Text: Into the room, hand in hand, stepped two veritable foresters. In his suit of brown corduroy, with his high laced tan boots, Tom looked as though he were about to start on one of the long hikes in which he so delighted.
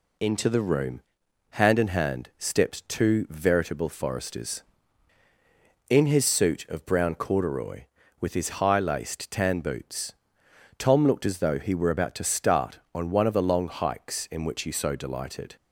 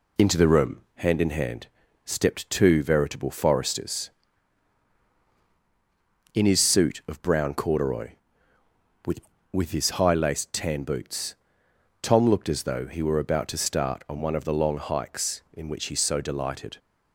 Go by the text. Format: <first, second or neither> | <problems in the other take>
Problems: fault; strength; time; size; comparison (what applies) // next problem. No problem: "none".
first | says "with" twice; at 9.5 s